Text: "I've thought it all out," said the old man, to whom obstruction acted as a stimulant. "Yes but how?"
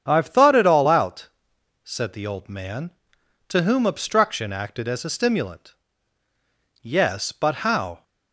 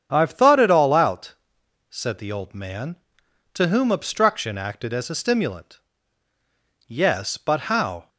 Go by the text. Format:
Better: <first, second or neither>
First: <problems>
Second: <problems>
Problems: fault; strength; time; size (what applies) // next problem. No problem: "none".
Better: neither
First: starts louder than the rest; strong; until 1.0 s; 8 dB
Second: starts louder than the rest; strong; until 1.1 s; 8 dB